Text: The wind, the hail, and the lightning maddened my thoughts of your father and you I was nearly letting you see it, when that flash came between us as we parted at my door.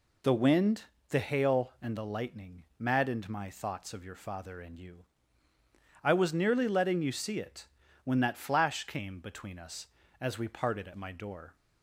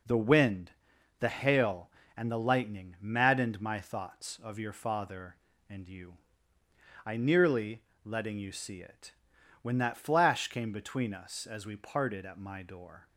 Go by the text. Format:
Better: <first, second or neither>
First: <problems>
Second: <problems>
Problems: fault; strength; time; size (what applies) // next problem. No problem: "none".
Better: first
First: pauses between "you" and "I"; noticeable; at 5.0 s; 0.98 s long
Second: pauses between "you" and "I"; noticeable; at 6.1 s; 0.92 s long // skips "was"; at 7.1 s // pauses between "nearly" and "letting"; slight; at 7.8 s; 0.22 s long